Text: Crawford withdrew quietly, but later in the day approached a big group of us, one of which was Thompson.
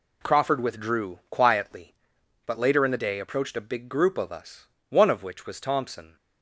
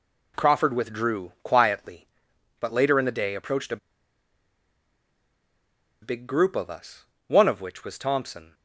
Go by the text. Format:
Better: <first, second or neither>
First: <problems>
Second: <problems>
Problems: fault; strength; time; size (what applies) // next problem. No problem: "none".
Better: first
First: none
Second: pauses between "a" and "big"; strong; at 3.7 s; 2.2 s long